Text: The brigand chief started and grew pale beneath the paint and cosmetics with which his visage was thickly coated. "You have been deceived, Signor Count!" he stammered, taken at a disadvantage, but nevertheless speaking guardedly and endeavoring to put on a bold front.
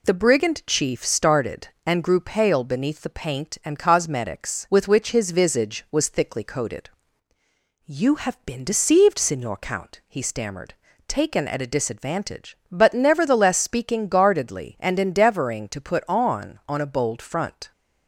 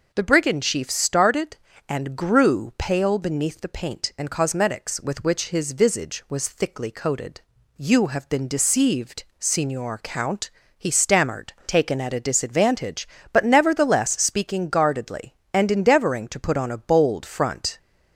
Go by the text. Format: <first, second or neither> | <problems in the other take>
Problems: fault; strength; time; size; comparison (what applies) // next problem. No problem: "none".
second | says "on" twice; at 16.6 s